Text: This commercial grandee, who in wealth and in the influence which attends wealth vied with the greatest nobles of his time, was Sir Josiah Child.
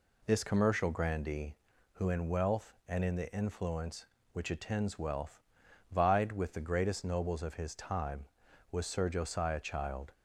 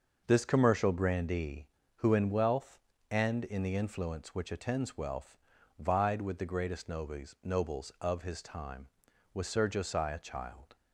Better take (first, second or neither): first